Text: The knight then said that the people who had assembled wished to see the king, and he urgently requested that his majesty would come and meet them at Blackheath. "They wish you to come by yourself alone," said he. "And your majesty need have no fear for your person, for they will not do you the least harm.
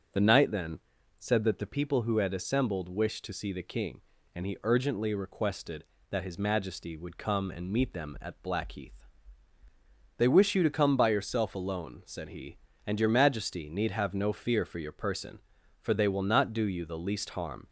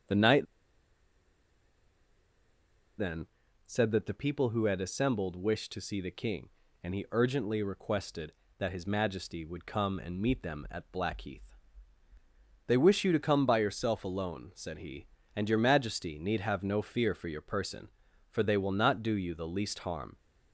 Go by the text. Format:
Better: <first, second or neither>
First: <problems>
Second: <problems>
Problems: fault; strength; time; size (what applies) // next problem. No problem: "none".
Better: first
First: starts louder than the rest; until 1.5 s; 7 dB // pauses between "then" and "said"; at 0.7 s; 0.40 s long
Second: starts louder than the rest; strong; until 4.0 s; 7 dB // pauses between "knight" and "then"; strong; at 0.4 s; 2.5 s long // pauses between "then" and "said"; at 3.2 s; 0.40 s long